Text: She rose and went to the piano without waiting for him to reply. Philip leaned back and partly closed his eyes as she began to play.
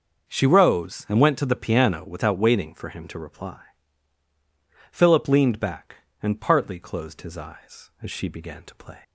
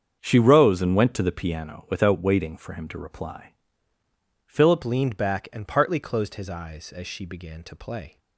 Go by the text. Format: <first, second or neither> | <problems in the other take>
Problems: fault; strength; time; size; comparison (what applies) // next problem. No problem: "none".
first | starts louder than the rest; strong; until 1.2 s; 7.5 dB; also in the first // changes voice at "leaned"; from 4.8 s on; 3.3 s long